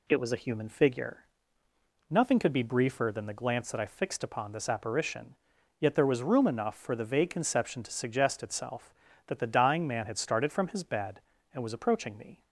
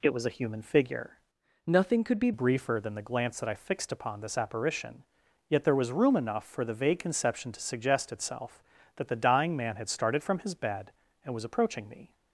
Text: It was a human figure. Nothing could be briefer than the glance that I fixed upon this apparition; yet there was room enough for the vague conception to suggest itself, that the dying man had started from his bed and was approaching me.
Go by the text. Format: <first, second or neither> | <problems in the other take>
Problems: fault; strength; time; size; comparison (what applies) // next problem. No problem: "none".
first | changes voice from "Nothing" to "be"; from 1.6 to 2.3 s; 0.7 s long